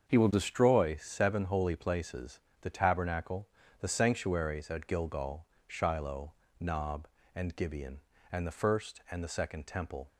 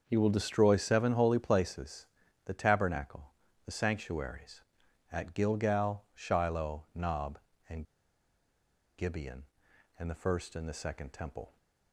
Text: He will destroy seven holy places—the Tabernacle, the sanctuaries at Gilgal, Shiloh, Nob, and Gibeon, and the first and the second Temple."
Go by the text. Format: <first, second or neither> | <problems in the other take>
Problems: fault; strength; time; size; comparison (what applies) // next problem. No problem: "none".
first | starts louder than the rest; until 1.0 s; 6.5 dB; also in the first // pauses between "and" and "Gibeon"; at 7.8 s; 1.1 s long